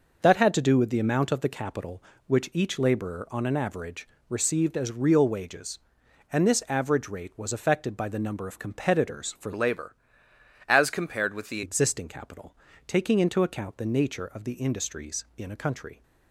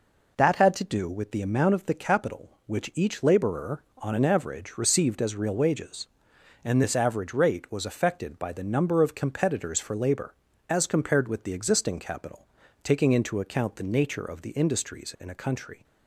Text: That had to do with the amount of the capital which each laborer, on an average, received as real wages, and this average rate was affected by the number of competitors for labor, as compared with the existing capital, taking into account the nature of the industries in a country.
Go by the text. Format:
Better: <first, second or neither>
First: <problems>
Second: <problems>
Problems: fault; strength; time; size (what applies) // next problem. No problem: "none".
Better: second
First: changes voice from "labor" to "the"; from 9.5 to 11.6 s; 2.1 s long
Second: none